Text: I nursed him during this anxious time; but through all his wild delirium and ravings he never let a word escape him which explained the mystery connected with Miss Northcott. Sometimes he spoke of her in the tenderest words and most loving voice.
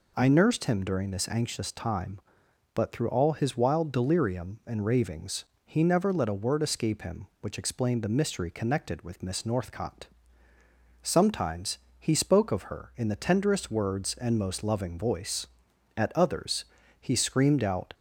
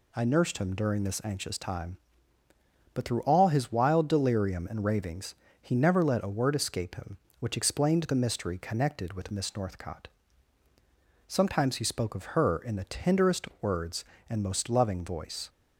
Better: second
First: pauses between "ravings" and "he"; slight; at 5.4 s; 0.22 s long // pauses between "Sometimes" and "he"; slight; at 11.7 s; 0.18 s long // goes on to say "At others he screamed out"; strong; from 15.9 s on; 1.9 s long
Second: pauses between "ravings" and "he"; slight; at 5.3 s; 0.28 s long

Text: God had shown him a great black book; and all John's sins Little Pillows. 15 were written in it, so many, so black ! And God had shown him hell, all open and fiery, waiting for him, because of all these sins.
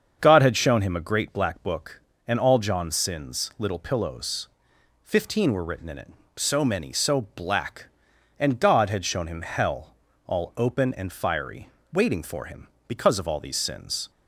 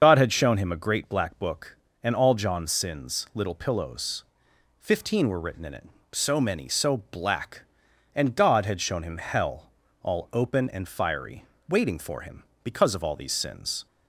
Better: first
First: starts louder than the rest; until 1.2 s; 7 dB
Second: loses the start of "God"; at 0.0 s; 60 ms // starts louder than the rest; until 1.0 s; 7 dB

